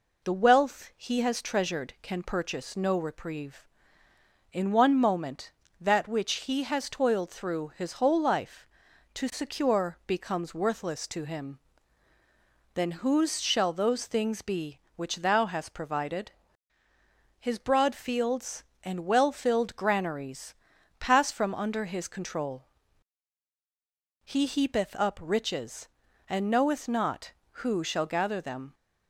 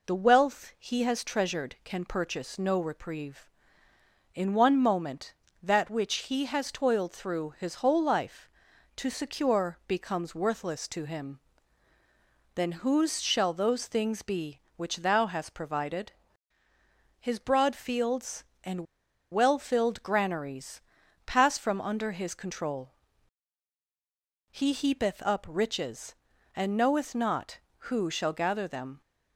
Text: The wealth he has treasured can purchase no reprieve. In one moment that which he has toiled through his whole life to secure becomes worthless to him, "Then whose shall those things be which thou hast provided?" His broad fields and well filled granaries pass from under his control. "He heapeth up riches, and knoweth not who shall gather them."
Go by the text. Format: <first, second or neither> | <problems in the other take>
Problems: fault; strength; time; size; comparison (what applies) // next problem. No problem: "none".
first | pauses between "and" and "well"; noticeable; at 18.8 s; 0.47 s long // pauses between "granaries" and "pass"; noticeable; at 20.8 s; 0.46 s long; noticeable in the first